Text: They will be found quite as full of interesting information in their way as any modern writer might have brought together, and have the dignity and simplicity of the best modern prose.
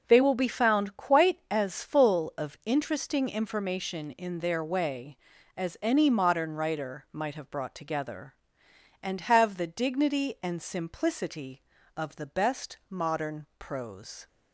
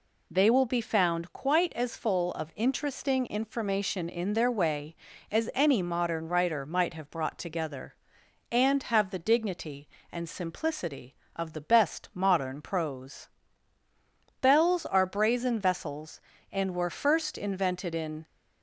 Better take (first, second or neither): first